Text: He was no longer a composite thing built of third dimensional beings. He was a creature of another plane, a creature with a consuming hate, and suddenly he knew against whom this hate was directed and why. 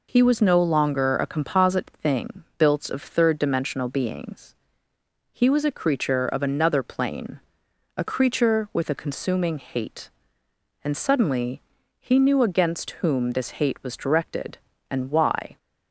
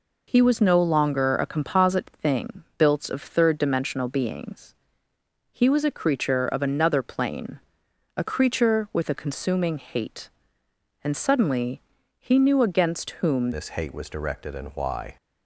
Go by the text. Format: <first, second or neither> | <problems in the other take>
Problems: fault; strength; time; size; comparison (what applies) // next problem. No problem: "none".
first | pauses between "suddenly" and "he"; at 11.8 s; 0.38 s long; also in the first // changes voice at "this"; from 13.5 s on; 1.6 s long